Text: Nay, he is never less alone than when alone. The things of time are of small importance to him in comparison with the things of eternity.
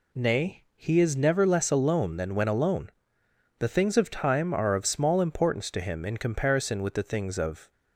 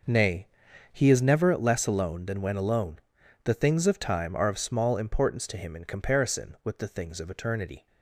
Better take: second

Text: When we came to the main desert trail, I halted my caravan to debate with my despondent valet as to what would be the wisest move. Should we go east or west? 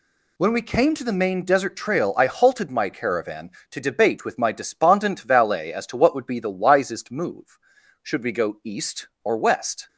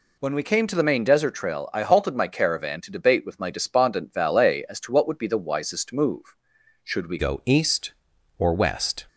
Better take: first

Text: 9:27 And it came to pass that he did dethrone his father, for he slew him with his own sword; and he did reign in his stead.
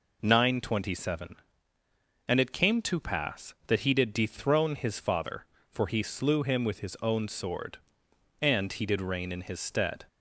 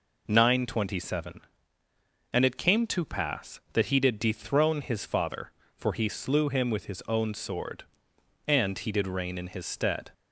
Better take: neither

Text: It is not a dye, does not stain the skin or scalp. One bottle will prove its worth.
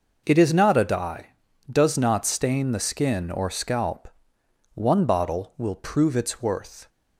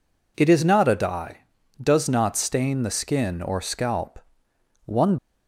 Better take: first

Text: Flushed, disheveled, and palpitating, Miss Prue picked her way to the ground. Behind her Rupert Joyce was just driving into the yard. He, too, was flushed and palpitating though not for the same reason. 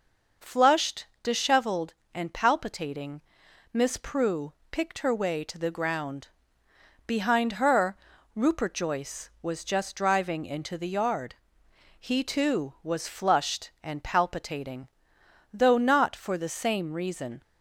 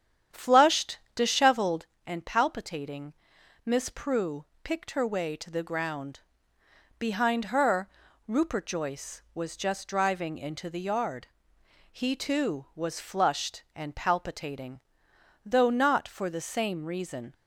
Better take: first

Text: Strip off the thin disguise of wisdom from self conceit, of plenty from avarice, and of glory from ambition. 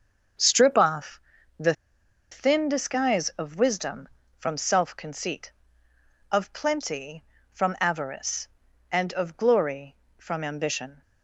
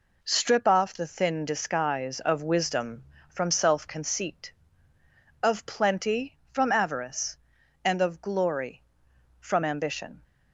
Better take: second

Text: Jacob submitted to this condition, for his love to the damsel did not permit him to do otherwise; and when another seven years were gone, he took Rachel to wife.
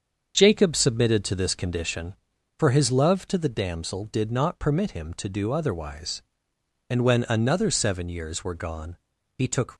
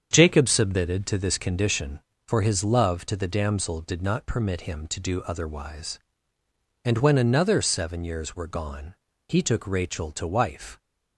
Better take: second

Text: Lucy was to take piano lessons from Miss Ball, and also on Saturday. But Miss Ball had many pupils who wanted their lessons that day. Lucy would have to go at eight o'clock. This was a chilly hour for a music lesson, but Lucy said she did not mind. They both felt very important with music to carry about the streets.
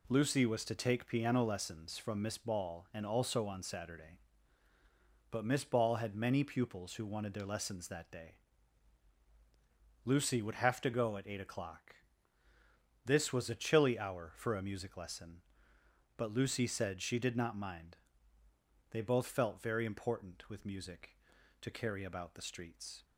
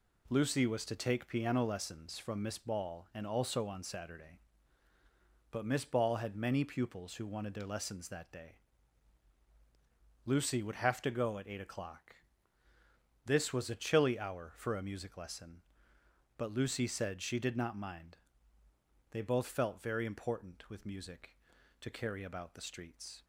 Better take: neither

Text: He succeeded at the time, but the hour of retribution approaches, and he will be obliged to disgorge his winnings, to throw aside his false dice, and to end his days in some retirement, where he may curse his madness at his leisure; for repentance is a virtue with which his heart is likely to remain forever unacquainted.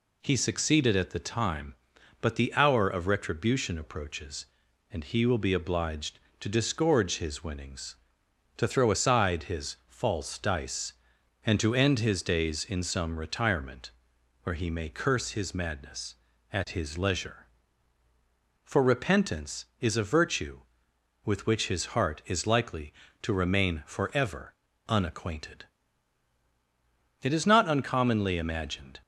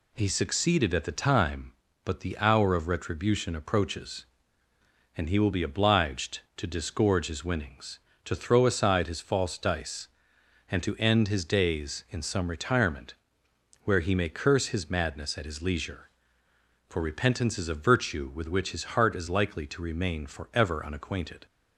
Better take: second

